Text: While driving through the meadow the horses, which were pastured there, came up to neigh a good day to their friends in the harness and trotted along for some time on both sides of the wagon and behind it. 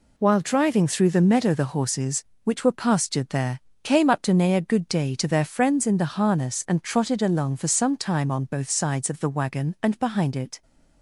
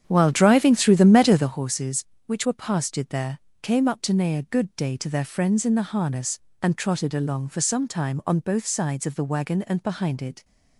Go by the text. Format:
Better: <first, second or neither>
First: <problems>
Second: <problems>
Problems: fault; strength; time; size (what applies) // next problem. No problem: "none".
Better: first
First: none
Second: starts louder than the rest; strong; until 1.6 s; 8.5 dB